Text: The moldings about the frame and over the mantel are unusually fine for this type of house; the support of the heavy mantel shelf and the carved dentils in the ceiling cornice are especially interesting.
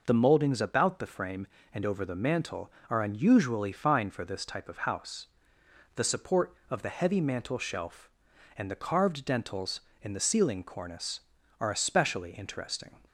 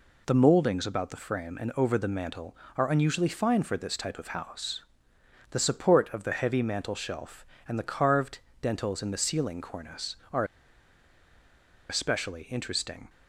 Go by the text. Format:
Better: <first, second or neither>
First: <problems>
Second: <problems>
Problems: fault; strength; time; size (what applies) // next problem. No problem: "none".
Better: first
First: none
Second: pauses between "carved" and "dentils"; slight; at 8.3 s; 0.24 s long // pauses between "are" and "especially"; strong; at 10.4 s; 1.4 s long